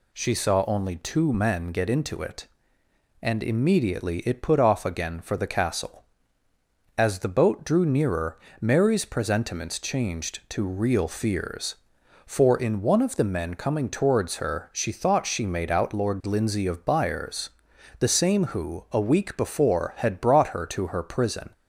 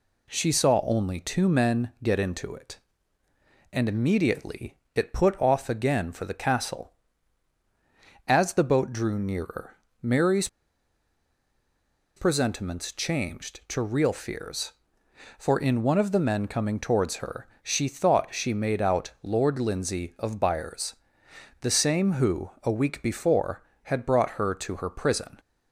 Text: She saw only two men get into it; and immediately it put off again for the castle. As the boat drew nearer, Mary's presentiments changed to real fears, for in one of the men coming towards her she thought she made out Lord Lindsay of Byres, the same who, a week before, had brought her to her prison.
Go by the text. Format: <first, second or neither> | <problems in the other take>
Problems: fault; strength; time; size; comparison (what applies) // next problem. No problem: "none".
first | pauses between "immediately" and "it"; slight; at 4.7 s; 0.18 s long // pauses between "Mary's" and "presentiments"; strong; at 10.4 s; 1.6 s long // pauses between "her" and "she"; slight; at 17.4 s; 0.16 s long